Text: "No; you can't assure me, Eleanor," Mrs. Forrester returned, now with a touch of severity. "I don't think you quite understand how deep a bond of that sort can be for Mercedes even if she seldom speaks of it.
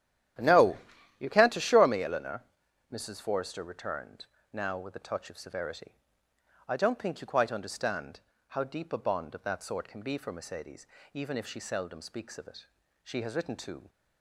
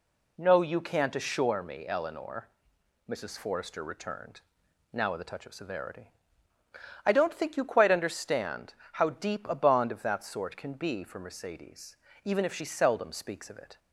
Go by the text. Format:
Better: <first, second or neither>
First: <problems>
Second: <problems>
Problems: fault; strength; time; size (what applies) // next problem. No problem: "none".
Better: second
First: starts louder than the rest; strong; until 1.7 s; 11.5 dB // pauses between "understand" and "how"; slight; at 8.2 s; 0.28 s long // pauses between "Mercedes" and "even"; slight; at 10.8 s; 0.28 s long // goes on to say "She has written to"; noticeable; from 13.0 s on; 0.88 s long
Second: pauses between "understand" and "how"; slight; at 8.7 s; 0.20 s long // pauses between "Mercedes" and "even"; slight; at 11.9 s; 0.28 s long